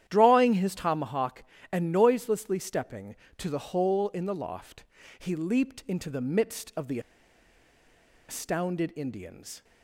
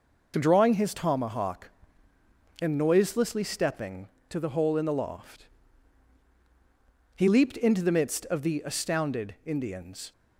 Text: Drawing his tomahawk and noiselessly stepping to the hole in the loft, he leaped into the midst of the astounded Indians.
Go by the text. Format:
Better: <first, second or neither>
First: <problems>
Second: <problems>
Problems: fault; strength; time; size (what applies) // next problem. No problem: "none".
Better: second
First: starts louder than the rest; strong; until 1.0 s; 11 dB // pauses between "the" and "astounded"; strong; at 6.9 s; 1.2 s long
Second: none